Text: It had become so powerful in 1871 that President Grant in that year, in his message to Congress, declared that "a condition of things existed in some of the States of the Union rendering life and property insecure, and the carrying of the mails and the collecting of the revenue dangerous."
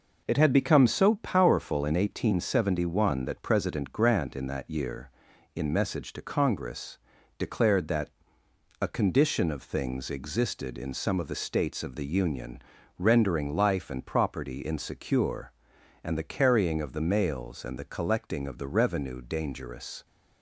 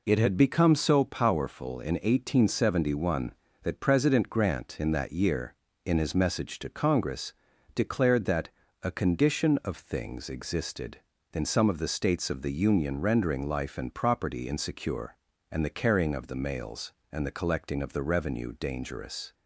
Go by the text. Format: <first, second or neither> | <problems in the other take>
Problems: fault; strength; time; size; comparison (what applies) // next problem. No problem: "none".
second | skips "his"; at 5.7 s // pauses between "that" and "a"; noticeable; at 8.0 s; 0.72 s long; slight in the second // pauses between "Union" and "rendering"; slight; at 12.6 s; 0.36 s long